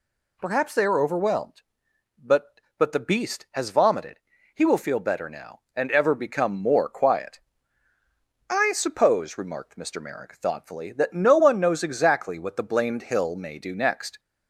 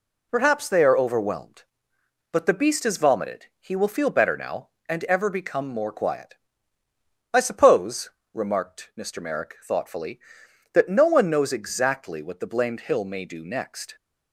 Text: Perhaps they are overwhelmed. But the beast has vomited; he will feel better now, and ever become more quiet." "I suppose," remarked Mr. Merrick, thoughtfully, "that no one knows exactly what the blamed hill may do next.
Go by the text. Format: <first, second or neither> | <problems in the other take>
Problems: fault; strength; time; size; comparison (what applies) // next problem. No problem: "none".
second | says "But" twice; at 2.7 s